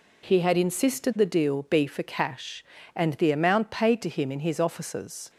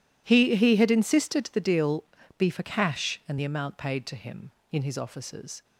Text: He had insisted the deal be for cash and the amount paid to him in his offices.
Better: first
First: none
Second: says "He" twice; at 0.5 s // pauses between "deal" and "be"; slight; at 2.0 s; 0.32 s long

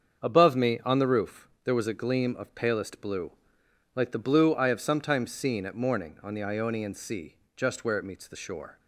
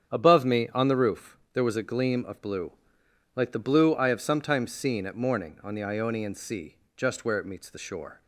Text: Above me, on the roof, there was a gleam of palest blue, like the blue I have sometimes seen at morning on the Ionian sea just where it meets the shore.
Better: first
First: starts louder than the rest; strong; until 1.2 s; 7 dB // pauses between "sea" and "just"; slight; at 7.3 s; 0.18 s long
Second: starts louder than the rest; strong; until 1.1 s; 8 dB // skips "palest"; at 2.4 s // pauses between "sea" and "just"; slight; at 6.7 s; 0.18 s long

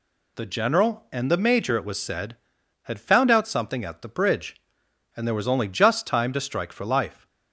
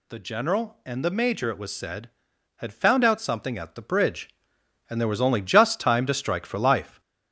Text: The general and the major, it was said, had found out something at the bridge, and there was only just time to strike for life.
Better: first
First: none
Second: gets louder; noticeable; throughout; 5 dB

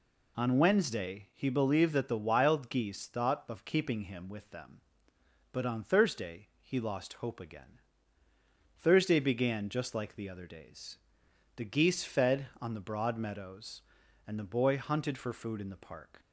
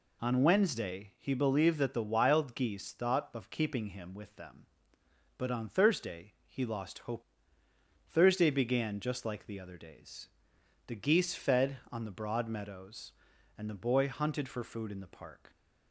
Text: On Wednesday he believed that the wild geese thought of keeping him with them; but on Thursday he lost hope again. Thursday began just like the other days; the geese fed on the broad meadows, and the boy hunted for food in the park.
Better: first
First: none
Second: skips "again"; at 7.6 s

